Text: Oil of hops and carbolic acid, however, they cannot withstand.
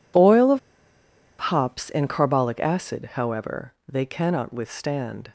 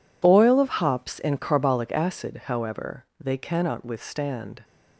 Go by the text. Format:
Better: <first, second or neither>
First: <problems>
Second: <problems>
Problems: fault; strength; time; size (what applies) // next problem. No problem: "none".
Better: second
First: pauses between "of" and "hops"; noticeable; at 0.5 s; 0.90 s long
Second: none